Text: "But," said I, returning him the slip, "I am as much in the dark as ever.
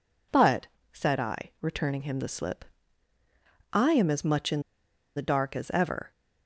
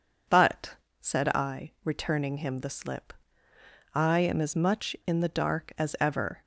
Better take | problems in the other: second | pauses between "in" and "the"; noticeable; at 4.6 s; 0.55 s long

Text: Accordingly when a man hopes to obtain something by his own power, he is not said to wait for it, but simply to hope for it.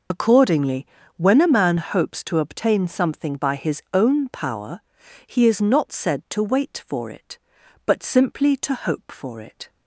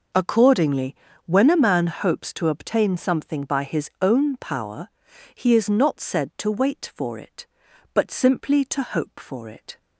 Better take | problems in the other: second | loses the start of "Accordingly"; at 0.1 s; 50 ms // pauses between "Accordingly" and "when"; slight; at 0.8 s; 0.32 s long; slight in the second

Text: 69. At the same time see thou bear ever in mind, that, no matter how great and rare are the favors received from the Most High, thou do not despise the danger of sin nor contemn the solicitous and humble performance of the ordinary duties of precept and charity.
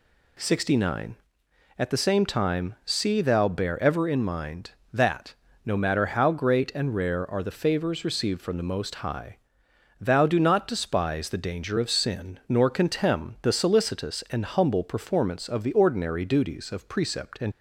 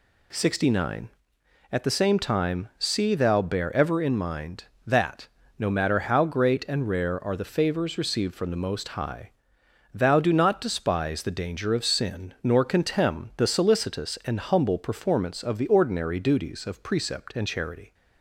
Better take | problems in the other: second | stops before "charity"; at 17.5 s

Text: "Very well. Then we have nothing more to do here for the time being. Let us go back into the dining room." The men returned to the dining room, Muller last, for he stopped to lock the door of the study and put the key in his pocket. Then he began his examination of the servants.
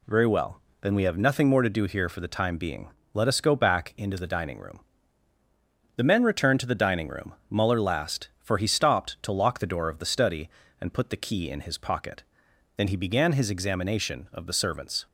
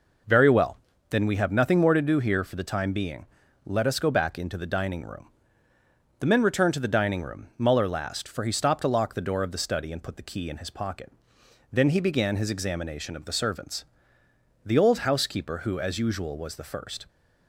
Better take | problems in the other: first | goes on to say "The old housekeeper who as usual was the first"; strong; from 14.6 s on; 2.4 s long

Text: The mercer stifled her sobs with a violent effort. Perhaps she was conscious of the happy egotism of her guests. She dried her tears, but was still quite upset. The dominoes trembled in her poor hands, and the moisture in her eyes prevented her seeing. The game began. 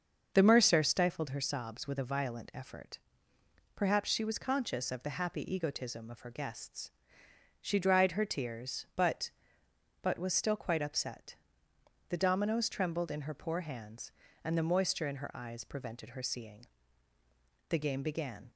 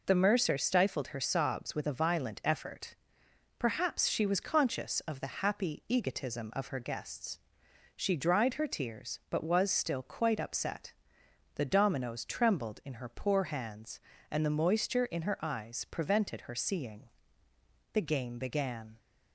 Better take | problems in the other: second | starts louder than the rest; until 1.3 s; 6.5 dB // says "but" twice; at 10.0 s

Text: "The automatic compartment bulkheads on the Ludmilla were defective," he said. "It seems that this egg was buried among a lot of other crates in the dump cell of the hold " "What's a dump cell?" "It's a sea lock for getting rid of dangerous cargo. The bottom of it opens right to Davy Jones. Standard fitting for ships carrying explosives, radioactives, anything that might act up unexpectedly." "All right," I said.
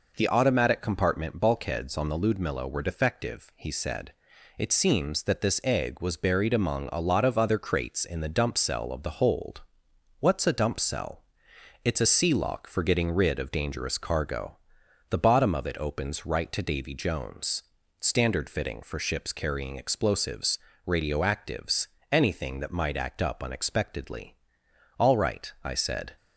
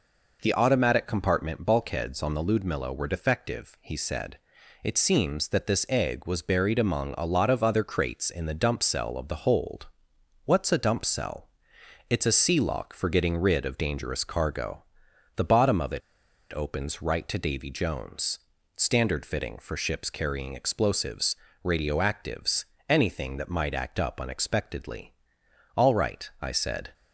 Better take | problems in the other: first | pauses between "it" and "opens"; noticeable; at 16.0 s; 0.52 s long

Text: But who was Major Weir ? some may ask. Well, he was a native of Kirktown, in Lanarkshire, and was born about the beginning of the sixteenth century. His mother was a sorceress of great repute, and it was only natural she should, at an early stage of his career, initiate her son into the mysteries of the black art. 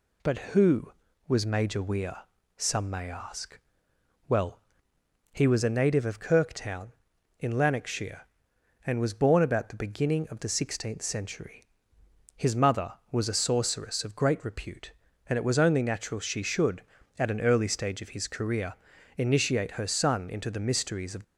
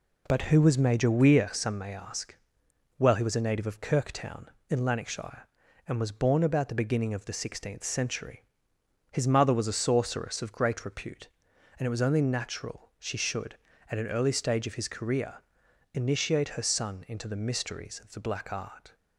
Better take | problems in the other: second | stops before "the black art"; at 21.2 s

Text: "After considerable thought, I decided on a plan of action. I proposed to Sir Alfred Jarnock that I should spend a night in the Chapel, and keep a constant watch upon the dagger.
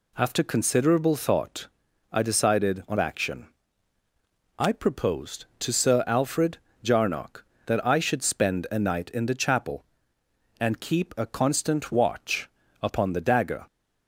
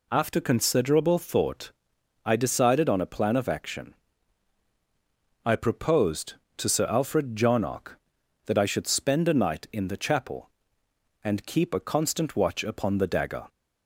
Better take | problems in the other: second | skips "a plan of"; at 2.9 s // pauses between "Alfred" and "Jarnock"; slight; at 6.5 s; 0.24 s long // pauses between "watch" and "upon"; slight; at 12.5 s; 0.32 s long

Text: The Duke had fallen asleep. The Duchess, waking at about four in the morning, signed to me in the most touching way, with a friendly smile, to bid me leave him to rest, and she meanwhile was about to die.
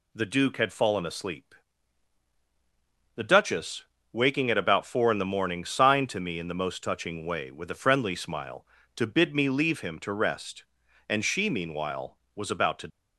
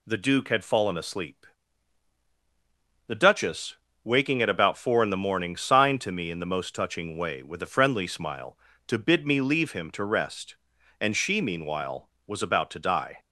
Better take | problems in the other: second | stops before "die"; at 12.8 s

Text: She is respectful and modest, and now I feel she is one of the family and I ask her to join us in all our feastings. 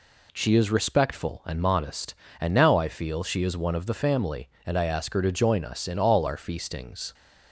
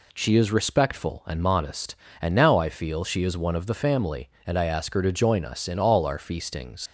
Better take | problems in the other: first | leaves "feastings" unfinished; at 6.8 s; 90 ms

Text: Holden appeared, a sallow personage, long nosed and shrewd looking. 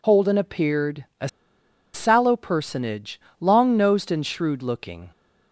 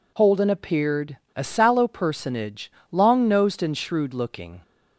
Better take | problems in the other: second | pauses between "a" and "sallow"; noticeable; at 1.2 s; 0.65 s long

